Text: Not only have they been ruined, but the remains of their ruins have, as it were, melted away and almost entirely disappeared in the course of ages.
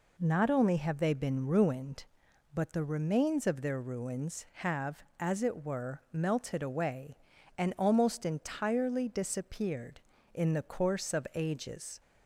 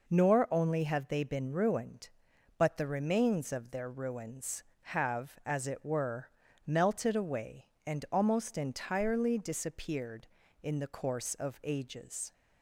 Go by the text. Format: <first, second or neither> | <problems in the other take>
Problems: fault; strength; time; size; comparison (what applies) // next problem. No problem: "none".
first | says "Nor" for "Not"; at 0.0 s